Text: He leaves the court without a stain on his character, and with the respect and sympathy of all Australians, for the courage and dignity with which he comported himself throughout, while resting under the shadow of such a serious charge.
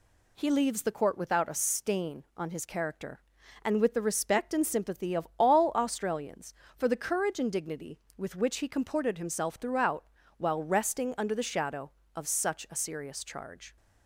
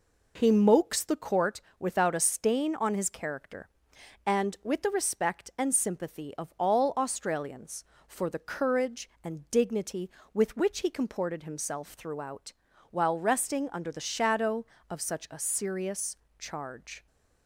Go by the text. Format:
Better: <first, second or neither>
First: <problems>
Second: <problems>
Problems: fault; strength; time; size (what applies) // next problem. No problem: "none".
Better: first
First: none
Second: says "mokes" for "leaves"; at 0.5 s // pauses between "court" and "without"; slight; at 1.6 s; 0.16 s long // pauses between "serious" and "charge"; slight; at 16.1 s; 0.22 s long